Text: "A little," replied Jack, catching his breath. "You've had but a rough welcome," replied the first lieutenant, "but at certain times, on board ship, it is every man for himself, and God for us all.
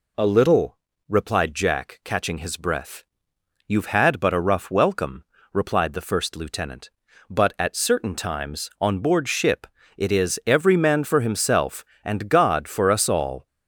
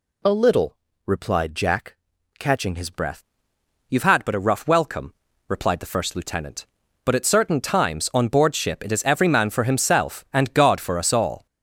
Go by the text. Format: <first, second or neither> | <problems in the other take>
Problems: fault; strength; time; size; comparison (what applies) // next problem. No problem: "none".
first | changes voice at "breath"; from 2.9 s on; 8.5 s long